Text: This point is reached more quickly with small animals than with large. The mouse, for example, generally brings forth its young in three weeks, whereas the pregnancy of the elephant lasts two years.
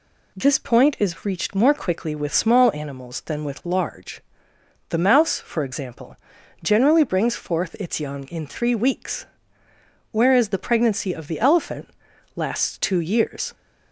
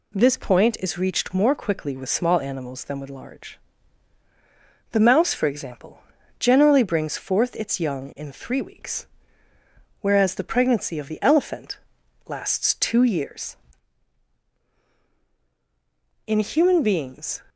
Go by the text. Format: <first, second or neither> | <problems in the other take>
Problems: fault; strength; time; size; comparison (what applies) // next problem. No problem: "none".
first | pauses between "elephant" and "lasts"; noticeable; at 11.7 s; 0.50 s long; noticeable in the first // goes on to say "In human beings"; noticeable; from 16.2 s on; 1.1 s long